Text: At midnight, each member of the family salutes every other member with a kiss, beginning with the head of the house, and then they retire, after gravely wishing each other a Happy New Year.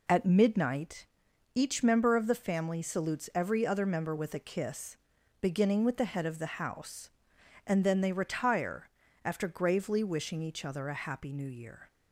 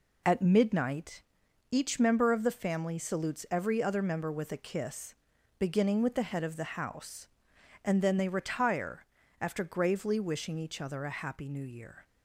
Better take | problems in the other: neither | none

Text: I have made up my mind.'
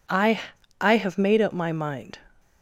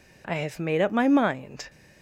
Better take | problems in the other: second | says "I" twice; at 0.8 s

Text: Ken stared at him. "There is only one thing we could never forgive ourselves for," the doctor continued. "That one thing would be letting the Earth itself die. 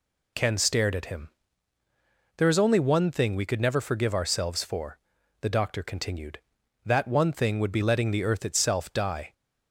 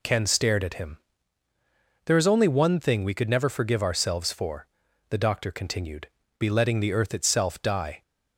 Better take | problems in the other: first | skips "That one thing would"; at 6.2 s

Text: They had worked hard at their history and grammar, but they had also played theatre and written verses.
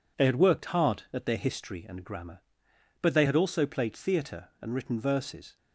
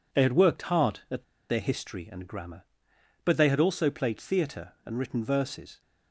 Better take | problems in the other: first | pauses between "at" and "their"; slight; at 1.2 s; 0.26 s long

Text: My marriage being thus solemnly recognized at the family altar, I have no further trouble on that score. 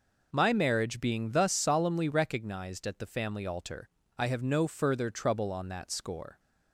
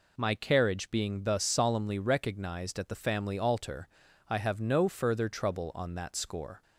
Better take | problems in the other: first | says "carriage" for "marriage"; at 0.3 s

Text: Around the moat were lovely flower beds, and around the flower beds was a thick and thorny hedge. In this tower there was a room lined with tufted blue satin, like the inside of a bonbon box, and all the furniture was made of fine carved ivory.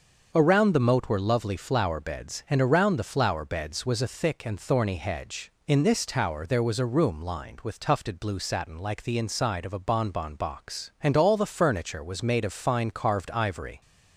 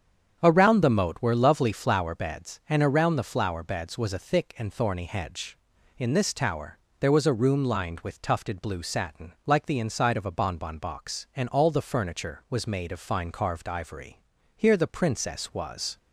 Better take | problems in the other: first | starts louder than the rest; strong; until 1.4 s; 8 dB; also in the first // pauses between "tower" and "there"; slight; at 6.7 s; 0.22 s long // goes on to say "Here the princess was"; from 14.5 s on; 1.4 s long

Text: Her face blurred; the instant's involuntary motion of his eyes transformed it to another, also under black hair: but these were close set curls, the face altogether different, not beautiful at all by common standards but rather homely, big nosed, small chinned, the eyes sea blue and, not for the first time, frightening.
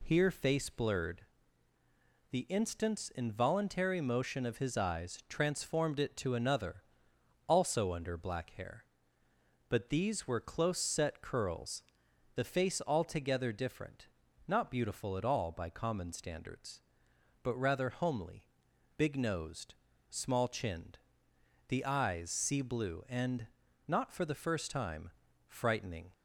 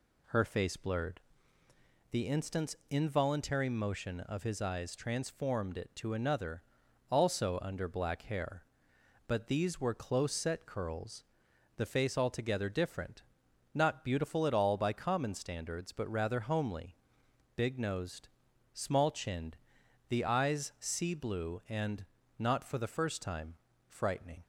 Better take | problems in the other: second | says "Here" for "Her"; at 0.0 s

